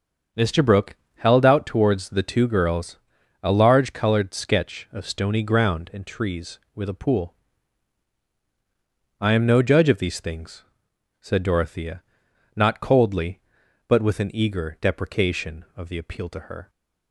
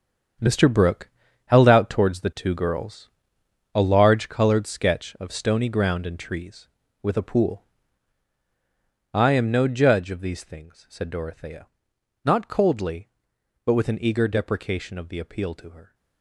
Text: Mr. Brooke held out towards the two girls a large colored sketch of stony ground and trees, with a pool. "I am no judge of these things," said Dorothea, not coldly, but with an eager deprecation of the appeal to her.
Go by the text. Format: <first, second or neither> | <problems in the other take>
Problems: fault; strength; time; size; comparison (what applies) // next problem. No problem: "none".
first | gets quieter; strong; throughout; 11 dB // starts louder than the rest; strong; until 1.7 s; 8 dB; also in the first // pauses between "Brooke" and "held"; at 1.0 s; 0.38 s long; slight in the first // pauses between "girls" and "a"; noticeable; at 3.0 s; 0.66 s long; noticeable in the first